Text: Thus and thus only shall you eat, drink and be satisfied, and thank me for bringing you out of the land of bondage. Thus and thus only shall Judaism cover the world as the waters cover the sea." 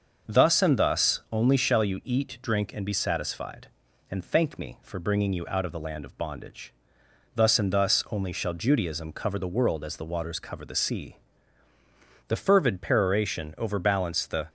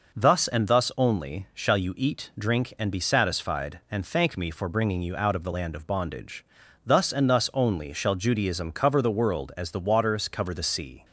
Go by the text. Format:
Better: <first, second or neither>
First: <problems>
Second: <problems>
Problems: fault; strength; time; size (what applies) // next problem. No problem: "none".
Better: second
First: starts louder than the rest; until 1.3 s; 6 dB // goes on to say "The fervid peroration overbalanced the"; strong; from 12.2 s on; 2.1 s long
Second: none